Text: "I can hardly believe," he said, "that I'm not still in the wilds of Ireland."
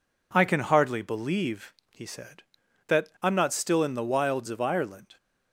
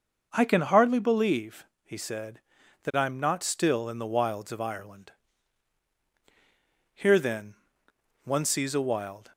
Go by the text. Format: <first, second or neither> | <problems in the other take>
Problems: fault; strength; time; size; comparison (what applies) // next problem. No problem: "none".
first | goes on to say "Here then one sees a wild"; strong; from 6.9 s on; 2.3 s long